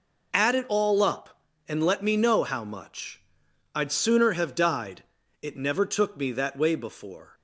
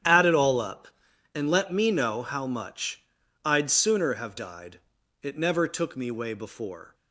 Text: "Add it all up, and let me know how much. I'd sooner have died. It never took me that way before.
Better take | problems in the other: first | starts louder than the rest; strong; until 1.4 s; 9.5 dB // skips "that"; at 6.0 s

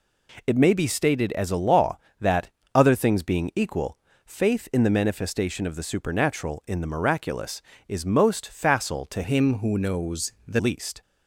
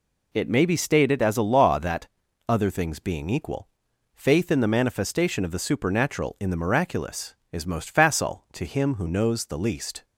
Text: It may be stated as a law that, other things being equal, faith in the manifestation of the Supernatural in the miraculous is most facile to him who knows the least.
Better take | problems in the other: second | changes voice from "him" to "the"; from 9.2 to 10.5 s; 1.3 s long

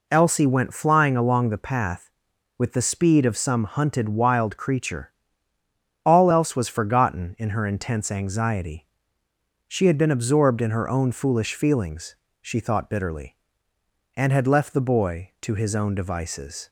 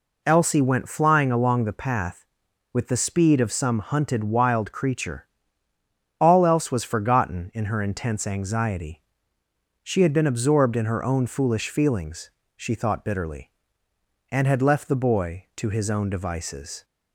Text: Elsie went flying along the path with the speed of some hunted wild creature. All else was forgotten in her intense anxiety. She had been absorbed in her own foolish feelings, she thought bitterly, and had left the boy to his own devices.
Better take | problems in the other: neither | none

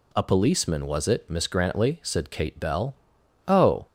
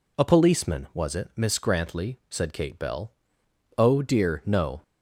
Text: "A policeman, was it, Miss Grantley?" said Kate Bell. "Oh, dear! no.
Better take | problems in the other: second | stops before "dear no"; at 3.8 s

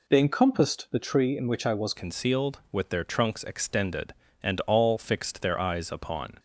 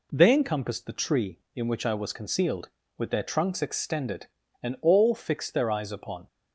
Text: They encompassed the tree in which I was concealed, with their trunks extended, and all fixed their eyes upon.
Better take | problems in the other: second | changes voice at "concealed"; from 1.9 s on; 4.4 s long

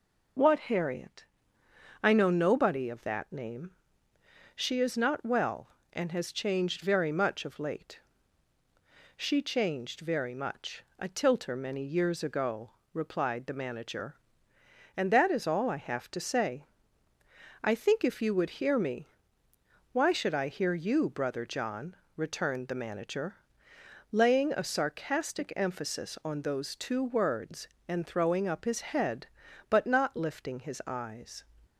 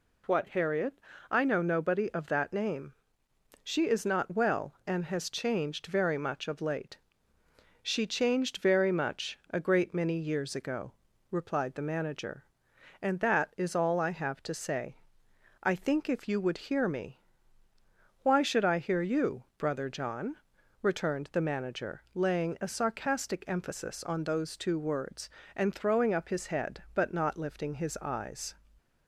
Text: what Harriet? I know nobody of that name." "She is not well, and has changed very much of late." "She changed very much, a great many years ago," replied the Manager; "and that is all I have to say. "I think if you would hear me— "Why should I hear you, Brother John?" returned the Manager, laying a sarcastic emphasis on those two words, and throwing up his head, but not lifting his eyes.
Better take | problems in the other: second | says "tilter" for "great"; at 11.0 s

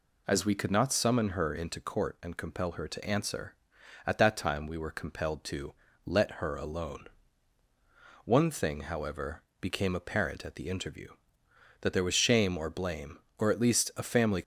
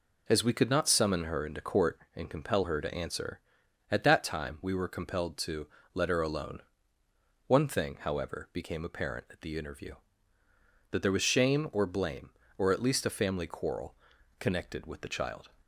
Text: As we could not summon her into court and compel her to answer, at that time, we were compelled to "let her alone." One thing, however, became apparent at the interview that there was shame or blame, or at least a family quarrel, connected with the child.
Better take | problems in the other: second | pauses between "to" and "let"; slight; at 5.7 s; 0.32 s long; slight in the second // stops before "quarrel connected with the child"; at 14.4 s

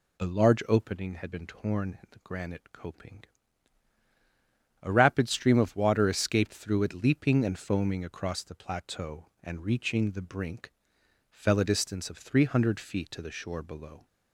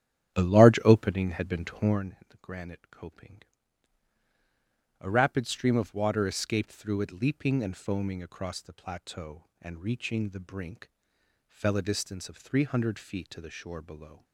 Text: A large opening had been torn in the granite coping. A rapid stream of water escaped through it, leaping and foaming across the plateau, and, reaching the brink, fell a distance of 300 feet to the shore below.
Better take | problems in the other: first | starts louder than the rest; strong; until 2.0 s; 10 dB

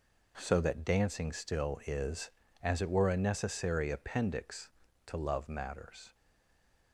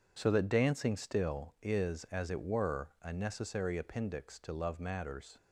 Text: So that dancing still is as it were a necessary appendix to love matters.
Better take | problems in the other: second | stays silent after the last word; slight; from 6.1 s on; 0.8 s long

